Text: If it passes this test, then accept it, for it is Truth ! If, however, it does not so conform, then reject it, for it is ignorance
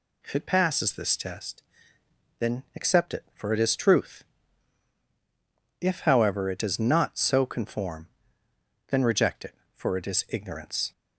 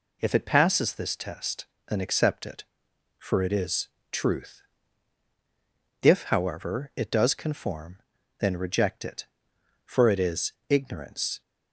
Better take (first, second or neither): first